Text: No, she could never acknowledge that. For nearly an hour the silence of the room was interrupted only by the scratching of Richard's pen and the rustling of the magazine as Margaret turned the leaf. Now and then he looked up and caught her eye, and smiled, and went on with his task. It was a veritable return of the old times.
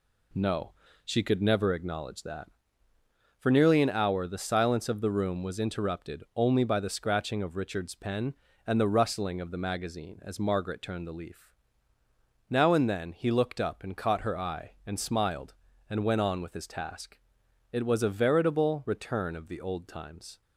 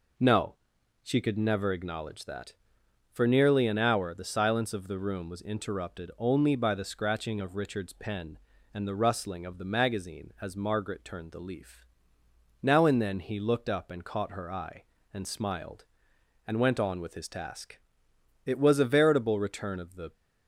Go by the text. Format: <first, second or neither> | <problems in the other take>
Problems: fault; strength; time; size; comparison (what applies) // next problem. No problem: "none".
first | stops before "old times"; at 20.1 s